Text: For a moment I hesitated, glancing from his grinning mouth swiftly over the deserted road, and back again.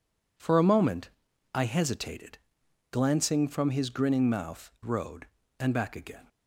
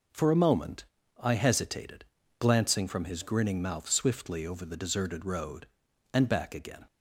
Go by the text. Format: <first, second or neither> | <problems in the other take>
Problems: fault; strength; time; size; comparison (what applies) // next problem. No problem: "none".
second | pauses between "moment" and "I"; at 1.1 s; 0.44 s long; slight in the second // skips "swiftly over the deserted"; at 4.7 s